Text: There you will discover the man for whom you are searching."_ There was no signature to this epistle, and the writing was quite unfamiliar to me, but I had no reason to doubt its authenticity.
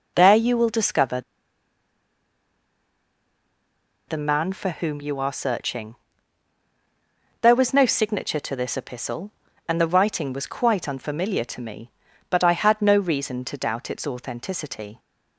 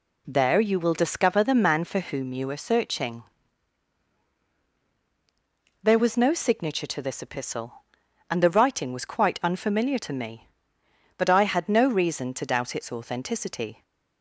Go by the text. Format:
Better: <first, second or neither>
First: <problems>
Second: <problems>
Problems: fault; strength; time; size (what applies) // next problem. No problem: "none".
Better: second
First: pauses between "discover" and "the"; strong; at 1.1 s; 2.8 s long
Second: none